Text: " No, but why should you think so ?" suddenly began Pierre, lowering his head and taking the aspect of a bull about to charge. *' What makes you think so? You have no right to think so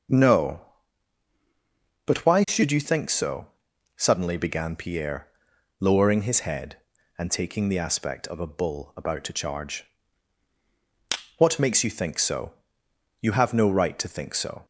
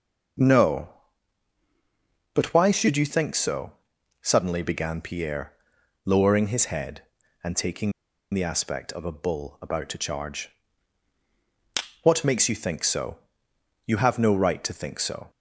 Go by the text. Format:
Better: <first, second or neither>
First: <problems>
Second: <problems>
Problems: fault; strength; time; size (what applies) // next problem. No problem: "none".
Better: first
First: starts louder than the rest; strong; until 2.5 s; 7.5 dB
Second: starts louder than the rest; strong; until 2.7 s; 7.5 dB // pauses between "taking" and "the"; at 7.9 s; 0.42 s long